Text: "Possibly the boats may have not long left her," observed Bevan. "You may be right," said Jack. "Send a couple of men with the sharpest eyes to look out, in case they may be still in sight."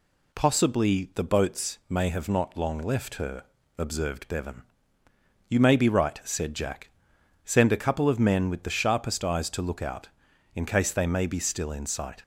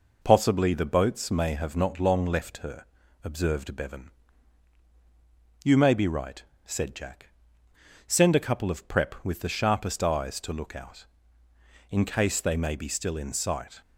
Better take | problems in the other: first | says "prep" for "men"; at 8.8 s

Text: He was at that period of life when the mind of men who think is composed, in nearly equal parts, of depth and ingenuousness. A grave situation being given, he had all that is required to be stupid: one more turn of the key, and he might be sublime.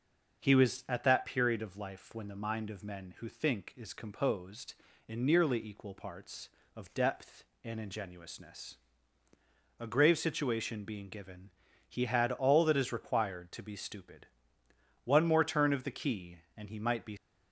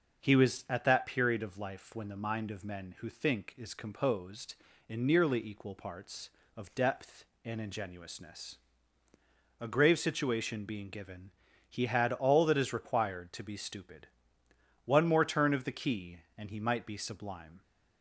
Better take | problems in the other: second | starts louder than the rest; until 1.4 s; 6 dB; also in the second // stops before "sublime"; at 17.1 s

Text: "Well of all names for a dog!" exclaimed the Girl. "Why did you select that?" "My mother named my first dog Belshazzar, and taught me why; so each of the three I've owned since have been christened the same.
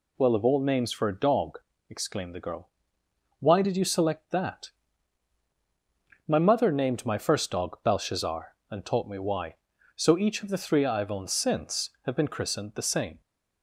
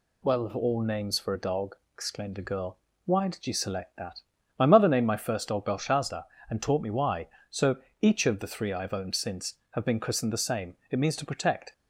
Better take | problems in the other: first | pauses between "so" and "each"; slight; at 7.7 s; 0.24 s long // goes on to say "It means to protect"; noticeable; from 10.9 s on; 0.82 s long

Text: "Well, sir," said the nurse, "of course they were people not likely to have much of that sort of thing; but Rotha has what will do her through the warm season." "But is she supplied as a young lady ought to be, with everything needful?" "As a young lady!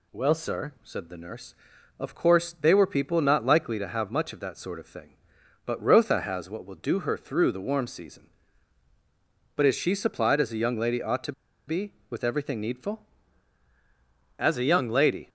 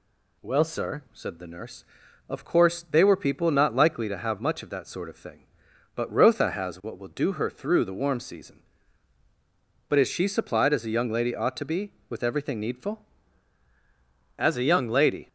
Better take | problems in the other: second | pauses between "to" and "be"; slight; at 11.3 s; 0.34 s long

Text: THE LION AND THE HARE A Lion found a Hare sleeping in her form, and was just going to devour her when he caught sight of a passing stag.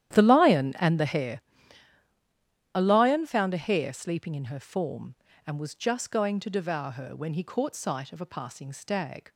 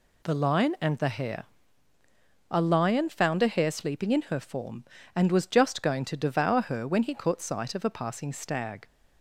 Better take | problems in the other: second | starts louder than the rest; strong; until 1.5 s; 11.5 dB // pauses between "HARE" and "A"; strong; at 1.3 s; 1.3 s long; also in the second

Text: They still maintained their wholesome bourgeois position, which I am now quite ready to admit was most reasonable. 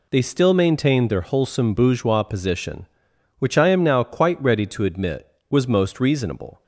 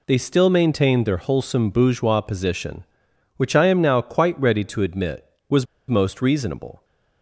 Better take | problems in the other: first | pauses between "was" and "most"; slight; at 5.6 s; 0.22 s long

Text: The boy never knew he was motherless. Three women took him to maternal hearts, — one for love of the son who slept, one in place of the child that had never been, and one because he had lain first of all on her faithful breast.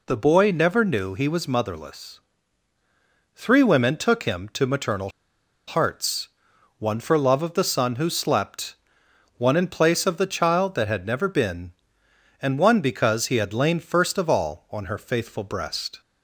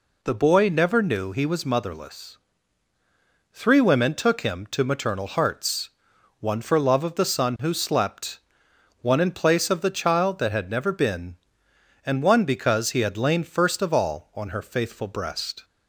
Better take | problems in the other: second | pauses between "maternal" and "hearts"; noticeable; at 5.0 s; 0.57 s long

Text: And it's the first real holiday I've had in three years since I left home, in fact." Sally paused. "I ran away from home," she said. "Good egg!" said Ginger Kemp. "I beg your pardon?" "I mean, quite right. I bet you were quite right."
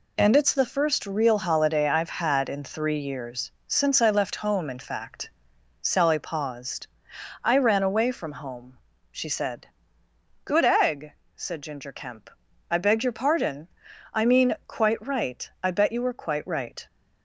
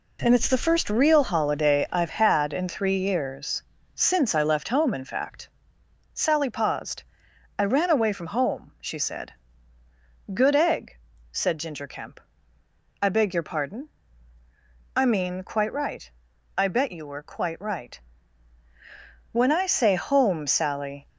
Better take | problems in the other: first | pauses between "years" and "since"; slight; at 3.6 s; 0.32 s long; slight in the first // goes on to say "When I say home Sally"; strong; from 19.3 s on; 1.7 s long

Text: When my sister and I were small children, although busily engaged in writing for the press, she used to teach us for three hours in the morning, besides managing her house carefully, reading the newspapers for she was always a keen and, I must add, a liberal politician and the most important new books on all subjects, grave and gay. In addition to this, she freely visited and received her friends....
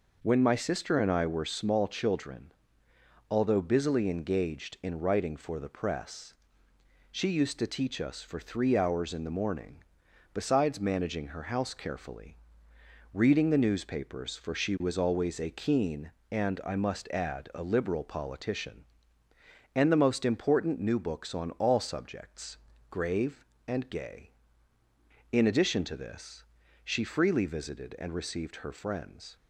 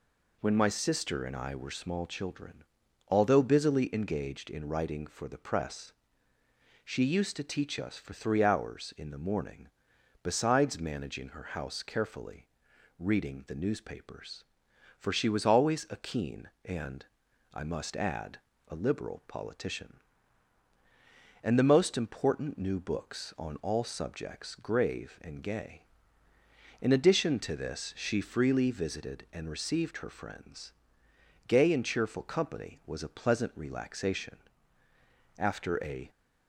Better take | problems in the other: first | goes on to say "Gay and cheerful company was a pleasant relaxation after a"; strong; from 31.4 s on; 4.6 s long

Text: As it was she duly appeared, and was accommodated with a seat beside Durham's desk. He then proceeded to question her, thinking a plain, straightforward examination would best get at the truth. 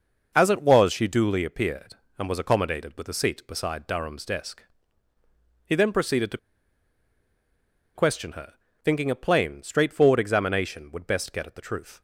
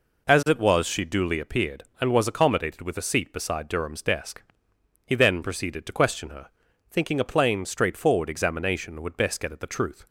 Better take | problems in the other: second | pauses between "to" and "question"; strong; at 6.3 s; 1.5 s long

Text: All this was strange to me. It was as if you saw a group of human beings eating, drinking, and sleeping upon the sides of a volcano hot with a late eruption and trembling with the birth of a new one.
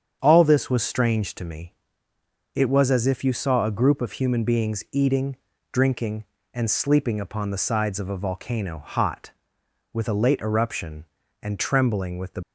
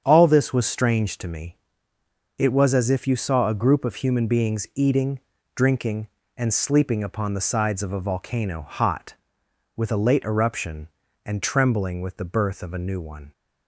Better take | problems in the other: second | starts louder than the rest; strong; until 1.2 s; 7.5 dB; strong in the second // stops before "birth of a new one"; at 12.4 s

